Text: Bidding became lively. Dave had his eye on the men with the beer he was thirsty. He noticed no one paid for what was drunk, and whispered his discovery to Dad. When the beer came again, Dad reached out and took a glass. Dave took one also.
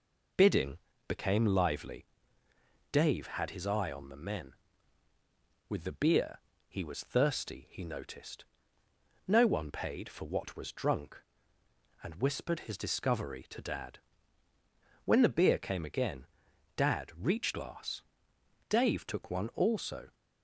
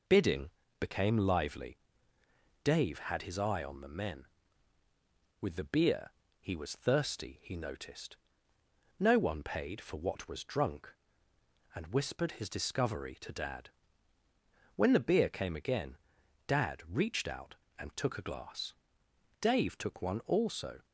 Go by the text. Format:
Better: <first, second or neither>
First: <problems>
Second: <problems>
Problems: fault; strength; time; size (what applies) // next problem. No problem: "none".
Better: second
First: pauses between "Bidding" and "became"; slight; at 0.7 s; 0.28 s long // pauses between "beer" and "he"; slight; at 6.3 s; 0.30 s long // pauses between "noticed" and "no"; noticeable; at 8.4 s; 0.84 s long // skips "out and took a"; at 17.5 s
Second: pauses between "Bidding" and "became"; slight; at 0.5 s; 0.28 s long // pauses between "beer" and "he"; slight; at 6.1 s; 0.30 s long // pauses between "noticed" and "no"; noticeable; at 8.1 s; 0.84 s long